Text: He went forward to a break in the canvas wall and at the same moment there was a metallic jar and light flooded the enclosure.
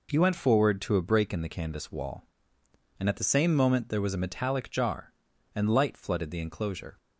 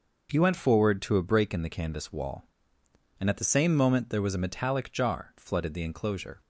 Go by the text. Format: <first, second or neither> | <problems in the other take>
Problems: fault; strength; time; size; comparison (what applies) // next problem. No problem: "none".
first | skips "and light"; at 5.3 s